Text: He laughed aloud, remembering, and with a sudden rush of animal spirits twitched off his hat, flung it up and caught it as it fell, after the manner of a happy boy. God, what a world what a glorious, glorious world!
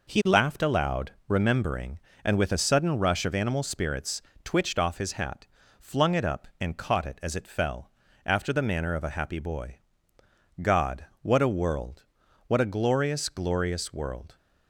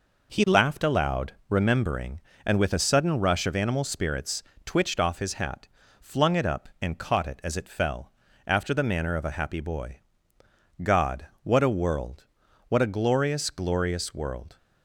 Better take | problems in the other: neither | pauses between "spirits" and "twitched"; slight; the same in both // pauses between "world" and "what"; the same in both

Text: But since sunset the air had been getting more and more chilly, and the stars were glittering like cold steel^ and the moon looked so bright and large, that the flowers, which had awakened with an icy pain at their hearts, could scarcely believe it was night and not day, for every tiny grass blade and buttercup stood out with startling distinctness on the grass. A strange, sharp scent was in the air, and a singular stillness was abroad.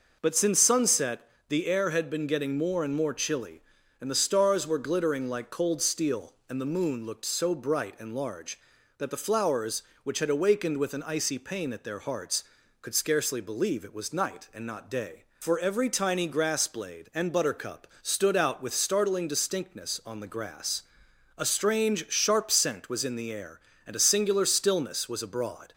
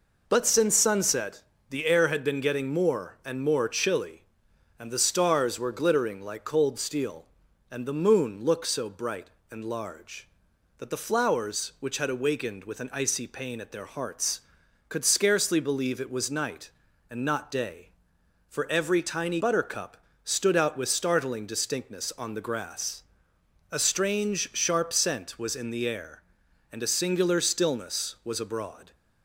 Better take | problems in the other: first | pauses between "sunset" and "the"; slight; at 1.4 s; 0.26 s long; slight in the first // skips "grass blade and"; at 19.4 s // pauses between "buttercup" and "stood"; slight; at 19.9 s; 0.26 s long

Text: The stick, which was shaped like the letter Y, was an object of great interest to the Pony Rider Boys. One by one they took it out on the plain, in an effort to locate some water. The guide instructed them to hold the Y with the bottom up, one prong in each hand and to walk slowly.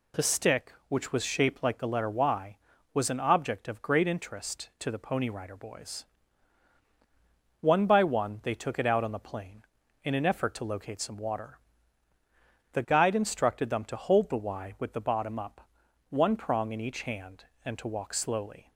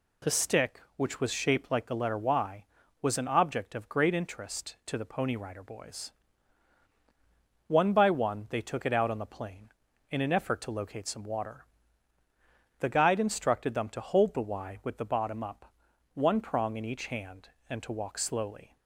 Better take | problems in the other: neither | none

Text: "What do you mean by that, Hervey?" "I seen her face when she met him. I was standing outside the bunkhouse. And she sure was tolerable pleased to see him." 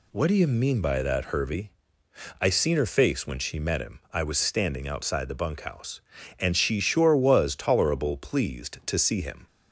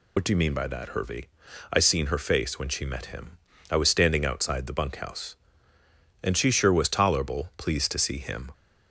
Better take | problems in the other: first | loses the start of "What"; at 0.1 s; 60 ms

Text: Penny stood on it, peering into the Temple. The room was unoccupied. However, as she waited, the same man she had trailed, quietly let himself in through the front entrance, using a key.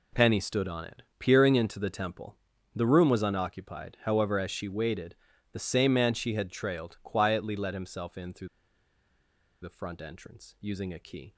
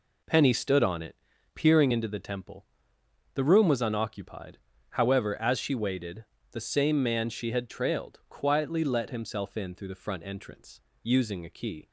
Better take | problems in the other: second | pauses between "through" and "the"; at 8.4 s; 1.1 s long

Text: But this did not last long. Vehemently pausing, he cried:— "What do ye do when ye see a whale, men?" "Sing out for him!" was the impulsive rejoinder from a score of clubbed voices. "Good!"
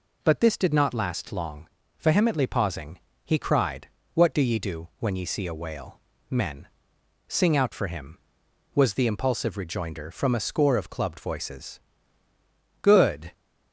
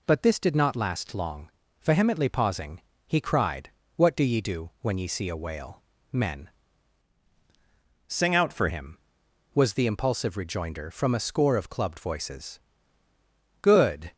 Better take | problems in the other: first | changes voice from "Sing" to "for"; from 8.0 to 8.6 s; 0.6 s long

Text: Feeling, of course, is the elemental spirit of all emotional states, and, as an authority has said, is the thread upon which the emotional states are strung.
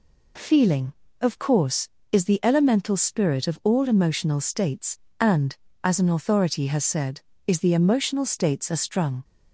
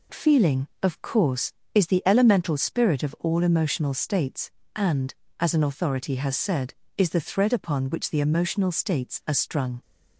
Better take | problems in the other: second | skips "thread upon which the"; at 7.7 s

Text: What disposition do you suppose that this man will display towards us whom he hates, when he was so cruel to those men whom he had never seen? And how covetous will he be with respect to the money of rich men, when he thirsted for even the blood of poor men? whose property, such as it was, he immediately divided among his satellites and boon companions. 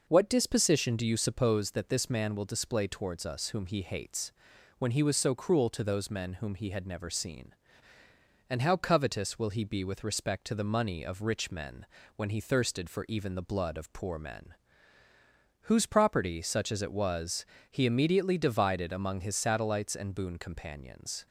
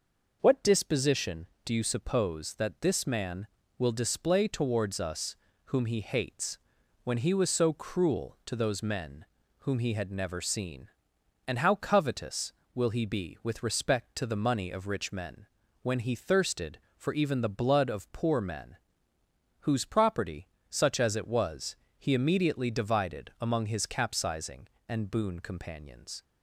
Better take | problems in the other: first | pauses between "us" and "whom"; slight; at 5.3 s; 0.30 s long // pauses between "men" and "whom"; slight; at 9.2 s; 0.34 s long // says "capsizing" for "satellites"; at 23.8 s

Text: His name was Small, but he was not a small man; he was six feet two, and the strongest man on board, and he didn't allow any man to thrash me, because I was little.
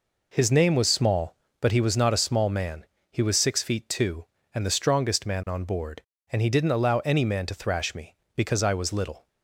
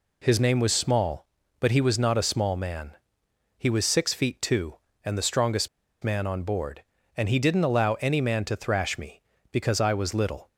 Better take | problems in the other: first | pauses between "strongest" and "man"; slight; at 5.6 s; 0.33 s long

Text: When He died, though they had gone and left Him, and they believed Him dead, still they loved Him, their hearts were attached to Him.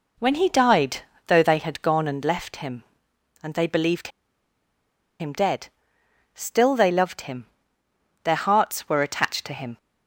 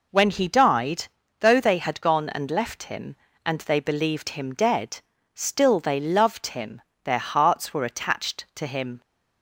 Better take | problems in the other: second | pauses between "believed" and "Him"; at 4.0 s; 1.1 s long

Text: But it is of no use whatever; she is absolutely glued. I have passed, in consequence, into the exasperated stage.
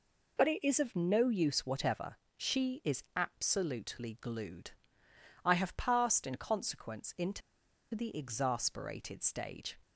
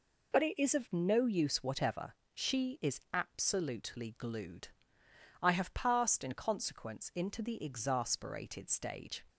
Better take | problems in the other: second | pauses between "into" and "the"; noticeable; at 7.4 s; 0.53 s long

